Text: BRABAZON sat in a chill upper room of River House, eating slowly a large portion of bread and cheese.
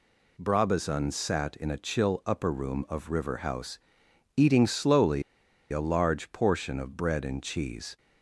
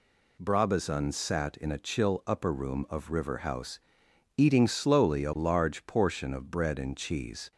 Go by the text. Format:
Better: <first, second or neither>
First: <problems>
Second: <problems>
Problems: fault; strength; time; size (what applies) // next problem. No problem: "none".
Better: second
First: pauses between "slowly" and "a"; noticeable; at 5.2 s; 0.48 s long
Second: none